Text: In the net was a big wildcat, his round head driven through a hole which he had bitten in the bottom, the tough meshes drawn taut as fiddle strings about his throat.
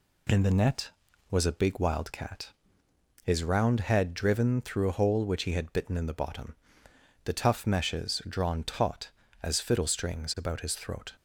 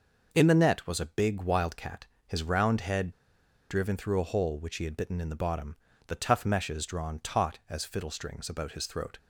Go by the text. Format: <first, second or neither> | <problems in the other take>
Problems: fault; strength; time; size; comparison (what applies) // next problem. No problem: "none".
first | pauses between "head" and "driven"; noticeable; at 3.1 s; 0.57 s long